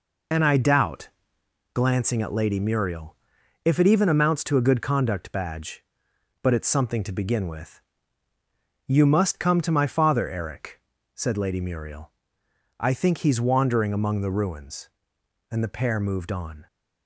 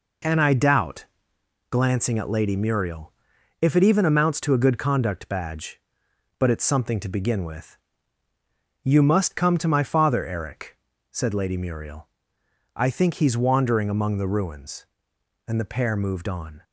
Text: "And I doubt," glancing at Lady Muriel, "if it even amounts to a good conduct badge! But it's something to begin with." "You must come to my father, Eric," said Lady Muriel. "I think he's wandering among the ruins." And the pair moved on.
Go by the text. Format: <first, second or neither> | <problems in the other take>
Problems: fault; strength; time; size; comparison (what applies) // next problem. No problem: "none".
second | loses the start of "And"; at 0.3 s; 55 ms